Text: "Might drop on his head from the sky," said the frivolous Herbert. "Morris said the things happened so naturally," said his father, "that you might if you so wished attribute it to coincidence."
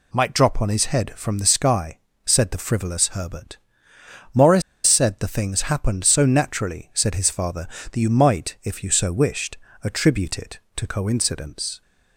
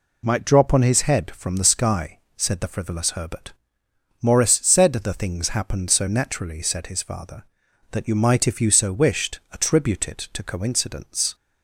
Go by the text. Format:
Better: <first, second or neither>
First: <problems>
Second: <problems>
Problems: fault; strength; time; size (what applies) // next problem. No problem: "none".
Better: second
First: pauses between "Morris" and "said"; slight; at 4.6 s; 0.25 s long // pauses between "wished" and "attribute"; slight; at 9.5 s; 0.26 s long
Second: none